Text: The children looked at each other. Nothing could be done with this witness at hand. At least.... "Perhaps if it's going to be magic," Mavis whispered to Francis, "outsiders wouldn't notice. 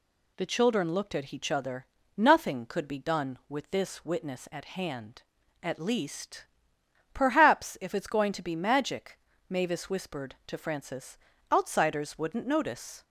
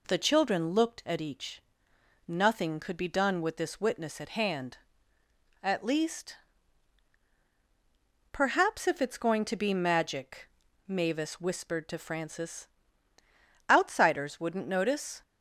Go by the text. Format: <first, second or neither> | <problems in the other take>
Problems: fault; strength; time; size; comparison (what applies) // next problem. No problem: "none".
first | skips "other"; at 1.9 s